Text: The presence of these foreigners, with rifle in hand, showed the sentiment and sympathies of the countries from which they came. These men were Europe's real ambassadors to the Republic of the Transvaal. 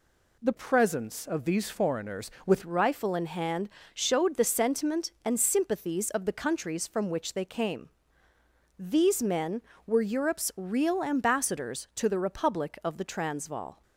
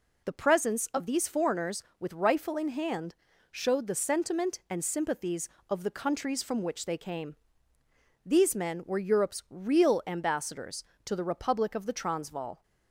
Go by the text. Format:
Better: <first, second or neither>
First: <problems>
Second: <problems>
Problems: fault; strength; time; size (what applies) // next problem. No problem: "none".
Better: second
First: changes voice from "presence" to "with"; from 0.5 to 2.6 s; 2.1 s long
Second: none